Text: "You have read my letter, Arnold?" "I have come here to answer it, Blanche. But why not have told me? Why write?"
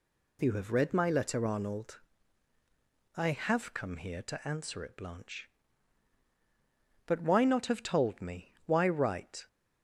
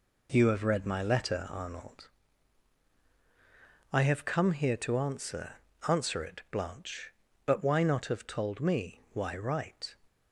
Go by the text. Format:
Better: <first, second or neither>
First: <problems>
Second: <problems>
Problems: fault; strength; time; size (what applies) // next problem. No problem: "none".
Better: first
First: none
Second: says "answer" twice; at 5.8 s